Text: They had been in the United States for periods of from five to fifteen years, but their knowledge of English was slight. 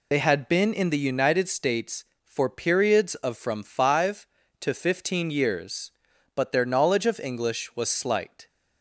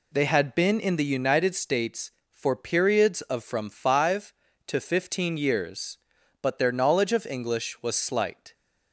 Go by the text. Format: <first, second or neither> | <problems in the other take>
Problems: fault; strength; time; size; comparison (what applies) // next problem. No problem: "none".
second | loses the start of "They"; at 0.1 s; 50 ms